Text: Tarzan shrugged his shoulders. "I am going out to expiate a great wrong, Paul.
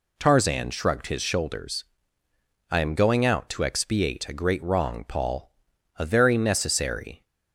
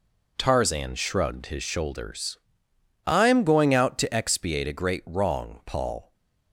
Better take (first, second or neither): second